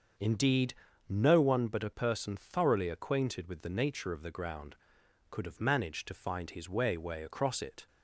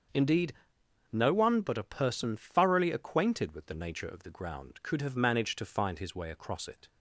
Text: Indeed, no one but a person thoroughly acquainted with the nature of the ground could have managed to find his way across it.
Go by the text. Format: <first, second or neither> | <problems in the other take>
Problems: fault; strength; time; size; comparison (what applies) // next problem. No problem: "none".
second | starts louder than the rest; until 1.5 s; 6.5 dB; also in the second // says "way" twice; at 6.9 s